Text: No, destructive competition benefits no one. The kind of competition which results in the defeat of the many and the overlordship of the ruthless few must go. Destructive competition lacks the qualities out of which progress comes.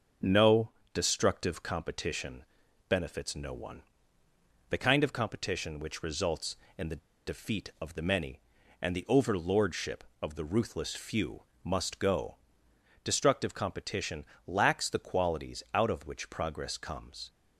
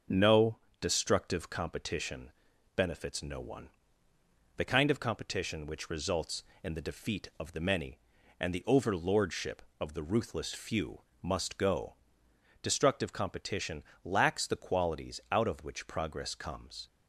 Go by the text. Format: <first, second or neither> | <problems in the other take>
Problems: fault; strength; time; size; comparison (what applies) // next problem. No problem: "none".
second | starts louder than the rest; noticeable; until 1.4 s; 6 dB; noticeable in the second // pauses between "competition" and "benefits"; at 2.4 s; 0.44 s long; also in the second // pauses between "the" and "defeat"; slight; at 6.9 s; 0.29 s long // pauses between "few" and "must"; slight; at 11.4 s; 0.20 s long; slight in the second // pauses between "competition" and "lacks"; slight; at 14.2 s; 0.22 s long; slight in the second